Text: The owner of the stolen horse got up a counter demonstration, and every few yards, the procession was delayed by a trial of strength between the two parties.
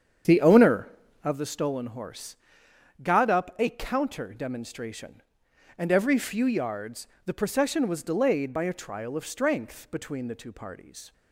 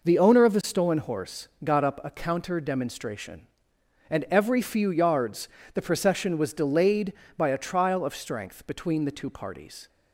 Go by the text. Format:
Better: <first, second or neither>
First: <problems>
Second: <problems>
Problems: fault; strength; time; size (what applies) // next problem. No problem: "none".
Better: second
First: starts louder than the rest; strong; until 1.4 s; 8 dB // pauses between "horse" and "got"; noticeable; at 2.3 s; 0.64 s long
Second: pauses between "horse" and "got"; slight; at 1.4 s; 0.16 s long